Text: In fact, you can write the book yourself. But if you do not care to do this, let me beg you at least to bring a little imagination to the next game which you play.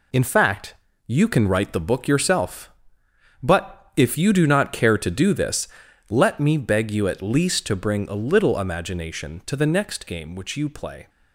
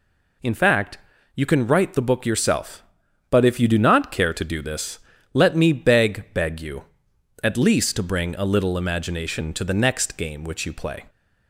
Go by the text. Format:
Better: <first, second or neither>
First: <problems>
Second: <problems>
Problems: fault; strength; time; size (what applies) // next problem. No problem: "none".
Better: first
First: none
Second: says "beg" twice; at 6.3 s